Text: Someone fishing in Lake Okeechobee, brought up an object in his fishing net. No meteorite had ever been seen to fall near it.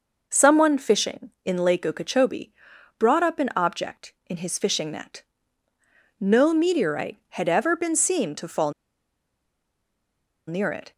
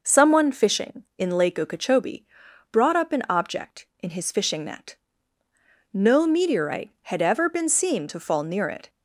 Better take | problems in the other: second | pauses between "fall" and "near"; strong; at 8.7 s; 1.7 s long

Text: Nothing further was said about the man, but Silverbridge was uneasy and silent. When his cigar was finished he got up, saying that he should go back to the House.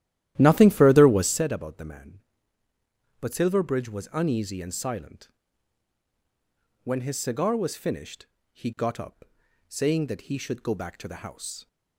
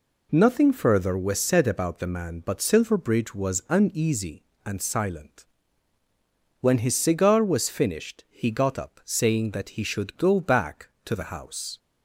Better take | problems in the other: second | starts louder than the rest; strong; until 1.4 s; 13 dB // pauses between "finished" and "he"; slight; at 8.2 s; 0.26 s long

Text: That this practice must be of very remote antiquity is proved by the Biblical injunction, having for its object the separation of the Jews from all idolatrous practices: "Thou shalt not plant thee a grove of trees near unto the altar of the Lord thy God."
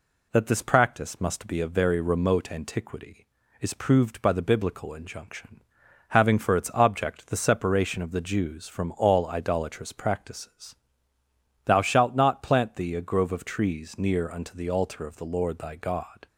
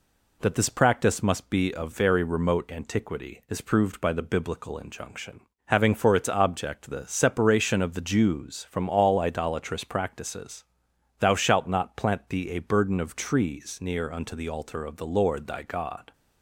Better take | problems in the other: first | says "burden" for "grove"; at 12.6 s

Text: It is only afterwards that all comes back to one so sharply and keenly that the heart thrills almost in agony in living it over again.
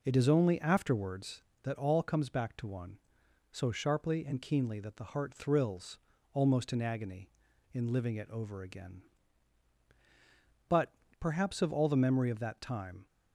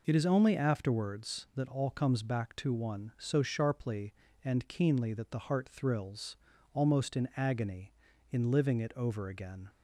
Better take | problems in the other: second | pauses between "thrills" and "almost"; slight; at 5.9 s; 0.36 s long; also in the second // goes on to say "But perhaps of all the memory of that time"; strong; from 10.6 s on; 2.3 s long

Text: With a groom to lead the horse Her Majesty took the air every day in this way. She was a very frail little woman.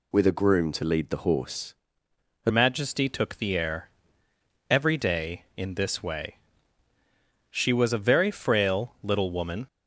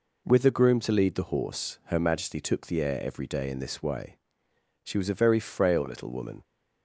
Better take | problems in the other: second | pauses between "horse" and "Her"; noticeable; at 1.7 s; 0.70 s long // changes voice at "Majesty"; from 2.5 s on; 7.1 s long // pauses between "air" and "every"; noticeable; at 3.8 s; 0.80 s long

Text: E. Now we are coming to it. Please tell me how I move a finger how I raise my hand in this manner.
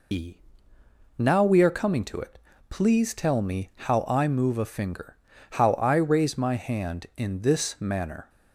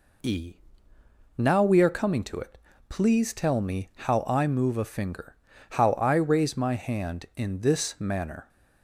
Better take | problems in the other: second | loses the start of "E"; at 0.1 s; 80 ms // pauses between "finger" and "how"; at 5.1 s; 0.38 s long; also in the second

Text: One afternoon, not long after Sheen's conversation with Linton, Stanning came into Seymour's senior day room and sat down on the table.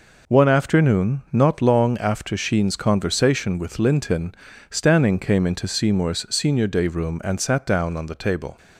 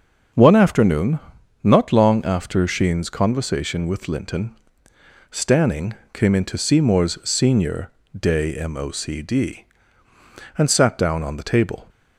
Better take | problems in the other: first | starts louder than the rest; until 1.7 s; 6.5 dB // pauses between "Stanning" and "came"; slight; at 5.9 s; 0.20 s long // pauses between "senior" and "day"; slight; at 7.9 s; 0.26 s long // says "mocd" for "room"; at 8.6 s

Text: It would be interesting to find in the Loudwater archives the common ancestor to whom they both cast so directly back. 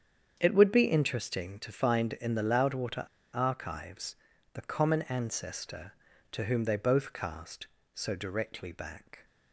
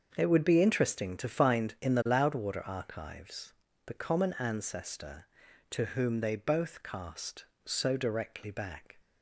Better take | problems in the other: second | starts louder than the rest; strong; until 1.4 s; 8 dB; also in the second // pauses between "Loudwater" and "archives"; slight; at 3.0 s; 0.27 s long // pauses between "archives" and "the"; at 4.1 s; 0.38 s long; slight in the second

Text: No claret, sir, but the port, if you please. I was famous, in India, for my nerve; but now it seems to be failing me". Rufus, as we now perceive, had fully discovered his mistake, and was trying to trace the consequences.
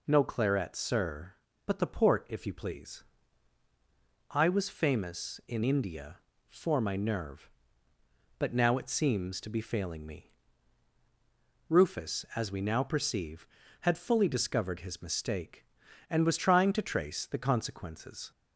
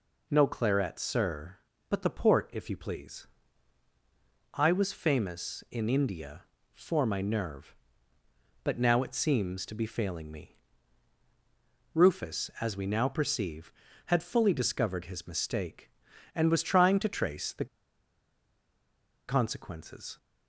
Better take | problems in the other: first | pauses between "the" and "consequences"; strong; at 17.6 s; 1.6 s long

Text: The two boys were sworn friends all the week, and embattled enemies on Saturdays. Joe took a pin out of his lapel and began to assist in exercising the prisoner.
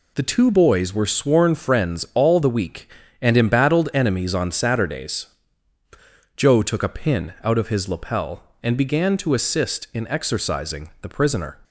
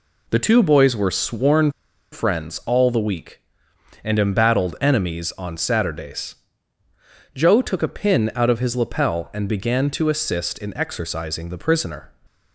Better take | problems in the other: first | pauses between "sworn" and "friends"; at 1.7 s; 0.40 s long

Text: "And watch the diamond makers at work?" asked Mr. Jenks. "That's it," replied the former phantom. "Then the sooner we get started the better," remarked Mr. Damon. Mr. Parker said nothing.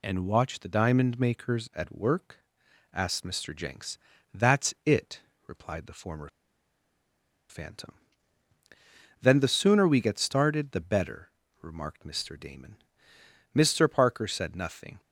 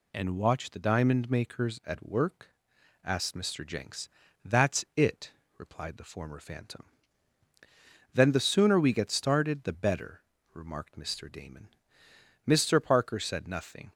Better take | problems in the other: second | pauses between "former" and "phantom"; at 6.2 s; 1.2 s long

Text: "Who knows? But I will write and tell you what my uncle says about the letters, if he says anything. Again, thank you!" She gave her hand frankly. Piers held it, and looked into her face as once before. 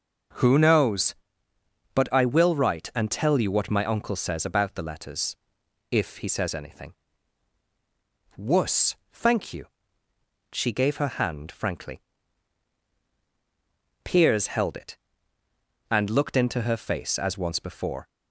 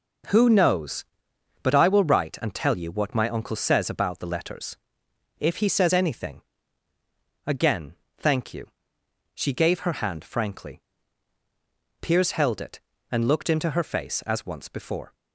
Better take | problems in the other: second | says "Wuss" for "Again"; at 8.3 s

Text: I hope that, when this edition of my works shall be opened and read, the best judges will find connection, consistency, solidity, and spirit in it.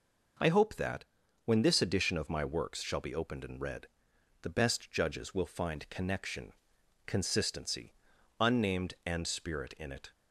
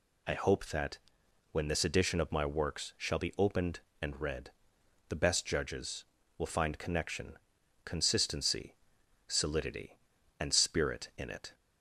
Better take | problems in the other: second | says "unnamed" for "solidity"; at 8.3 s

